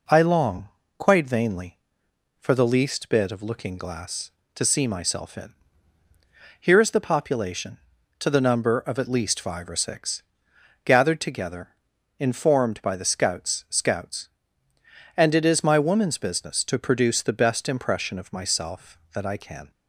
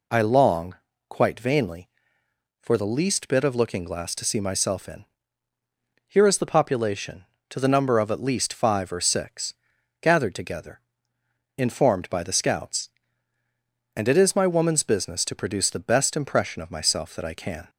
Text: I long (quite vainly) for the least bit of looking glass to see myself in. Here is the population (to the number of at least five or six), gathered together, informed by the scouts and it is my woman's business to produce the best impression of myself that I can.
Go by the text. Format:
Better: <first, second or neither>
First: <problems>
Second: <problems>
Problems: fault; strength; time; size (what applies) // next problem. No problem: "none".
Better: second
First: says "scouts" twice; at 13.6 s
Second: none